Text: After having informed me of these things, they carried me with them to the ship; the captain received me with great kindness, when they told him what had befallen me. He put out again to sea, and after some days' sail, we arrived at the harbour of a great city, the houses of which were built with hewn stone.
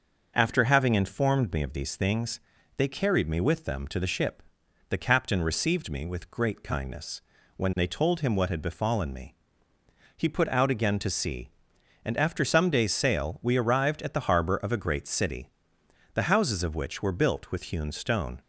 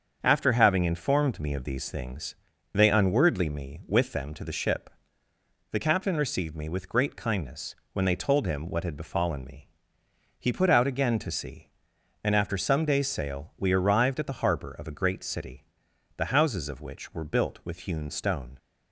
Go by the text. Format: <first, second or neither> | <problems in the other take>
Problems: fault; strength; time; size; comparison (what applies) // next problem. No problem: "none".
first | starts louder than the rest; until 1.2 s; 7 dB; also in the first // says "unwordly" for "carried"; at 2.8 s